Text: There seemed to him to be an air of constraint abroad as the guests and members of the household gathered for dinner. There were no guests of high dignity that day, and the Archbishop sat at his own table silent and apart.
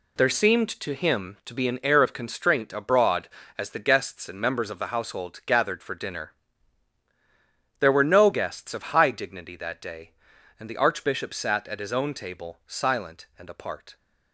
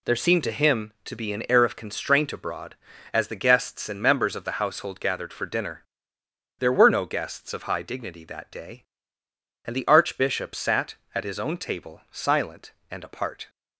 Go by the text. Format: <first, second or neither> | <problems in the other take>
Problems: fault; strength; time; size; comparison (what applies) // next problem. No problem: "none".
second | gets quieter; strong; throughout; 8.5 dB